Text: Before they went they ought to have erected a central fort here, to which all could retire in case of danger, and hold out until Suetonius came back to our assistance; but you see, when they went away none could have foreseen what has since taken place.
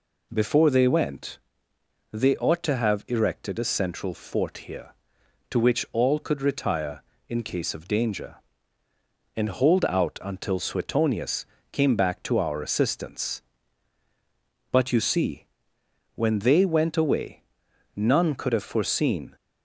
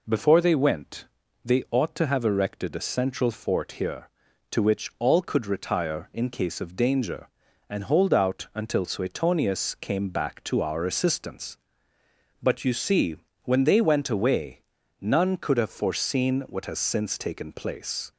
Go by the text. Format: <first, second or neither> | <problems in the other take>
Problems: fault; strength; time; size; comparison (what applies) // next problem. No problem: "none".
second | pauses between "went" and "they"; noticeable; at 1.3 s; 0.72 s long; also in the second // pauses between "Suetonius" and "came"; slight; at 11.4 s; 0.26 s long // pauses between "away" and "none"; noticeable; at 17.4 s; 0.52 s long; also in the second // stops before "what has since taken place"; at 19.3 s